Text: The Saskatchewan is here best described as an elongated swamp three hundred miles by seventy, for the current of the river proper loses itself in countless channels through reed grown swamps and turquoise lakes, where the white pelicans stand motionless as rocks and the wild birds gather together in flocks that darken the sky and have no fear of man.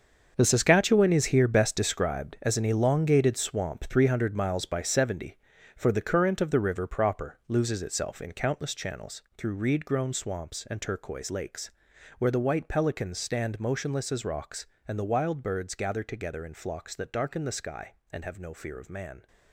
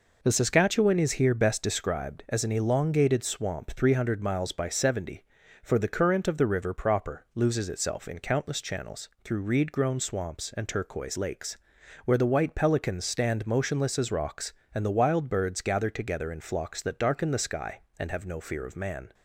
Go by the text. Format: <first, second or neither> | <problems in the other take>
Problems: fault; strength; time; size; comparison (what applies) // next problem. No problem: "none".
second | gets quieter; strong; throughout; 11.5 dB // pauses between "channels" and "through"; slight; at 9.2 s; 0.16 s long; slight in the second